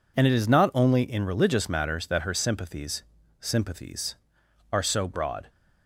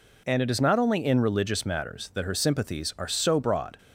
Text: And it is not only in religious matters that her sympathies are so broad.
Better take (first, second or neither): second